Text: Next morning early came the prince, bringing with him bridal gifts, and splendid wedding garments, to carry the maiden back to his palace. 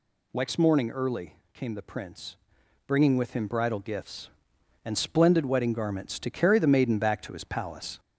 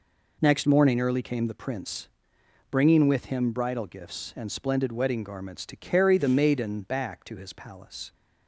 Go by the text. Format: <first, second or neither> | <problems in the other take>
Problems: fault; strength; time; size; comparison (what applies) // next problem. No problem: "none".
second | gets louder; slight; throughout; 2.5 dB // pauses between "early" and "came"; slight; at 1.3 s; 0.16 s long